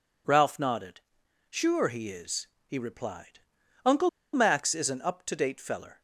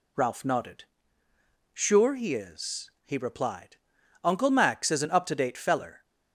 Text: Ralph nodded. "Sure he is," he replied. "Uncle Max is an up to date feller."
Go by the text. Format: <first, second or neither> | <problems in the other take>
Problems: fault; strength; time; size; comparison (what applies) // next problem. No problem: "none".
second | pauses between "Uncle" and "Max"; slight; at 4.0 s; 0.24 s long